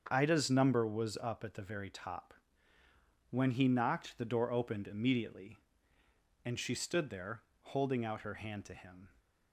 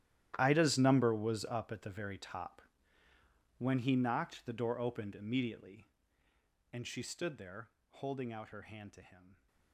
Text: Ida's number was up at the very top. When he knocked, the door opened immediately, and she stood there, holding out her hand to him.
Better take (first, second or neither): first